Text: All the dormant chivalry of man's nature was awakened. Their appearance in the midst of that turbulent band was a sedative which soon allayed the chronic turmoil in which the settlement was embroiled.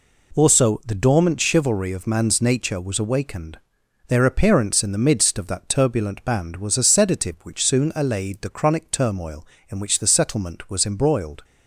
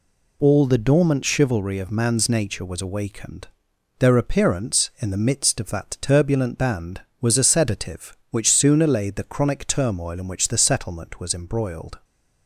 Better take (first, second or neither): second